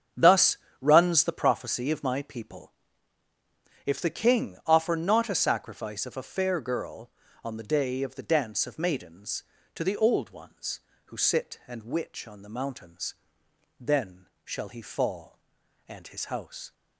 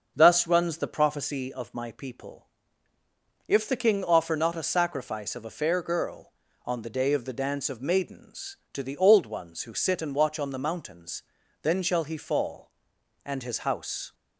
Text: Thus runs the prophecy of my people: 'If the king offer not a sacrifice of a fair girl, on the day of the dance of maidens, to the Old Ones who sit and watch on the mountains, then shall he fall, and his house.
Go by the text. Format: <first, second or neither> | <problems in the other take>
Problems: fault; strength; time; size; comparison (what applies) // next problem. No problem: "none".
second | starts louder than the rest; strong; until 1.3 s; 7.5 dB; also in the second // pauses between "Thus" and "runs"; slight; at 0.5 s; 0.24 s long // says "witch" for "watch"; at 11.8 s // pauses between "then" and "shall"; slight; at 14.2 s; 0.18 s long